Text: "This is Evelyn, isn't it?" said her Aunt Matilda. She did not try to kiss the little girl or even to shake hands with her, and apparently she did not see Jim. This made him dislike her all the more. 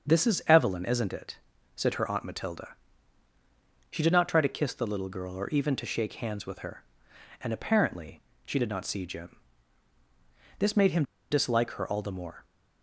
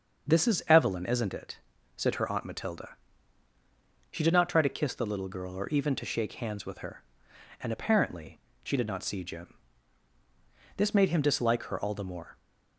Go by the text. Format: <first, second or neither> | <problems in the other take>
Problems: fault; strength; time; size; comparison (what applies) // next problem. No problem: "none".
second | starts louder than the rest; until 1.1 s; 6.5 dB; also in the second // pauses between "apparently" and "she"; slight; at 8.2 s; 0.22 s long; slight in the second // pauses between "him" and "dislike"; slight; at 11.0 s; 0.28 s long